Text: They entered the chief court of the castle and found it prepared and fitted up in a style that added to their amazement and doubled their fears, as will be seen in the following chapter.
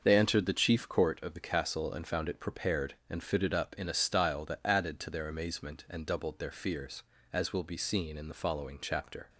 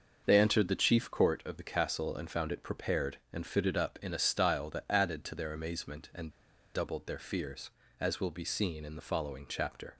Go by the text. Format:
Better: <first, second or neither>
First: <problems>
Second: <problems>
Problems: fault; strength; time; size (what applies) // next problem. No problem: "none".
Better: first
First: starts louder than the rest; until 1.0 s; 6 dB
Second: starts louder than the rest; until 1.2 s; 6 dB // pauses between "and" and "doubled"; at 6.2 s; 0.44 s long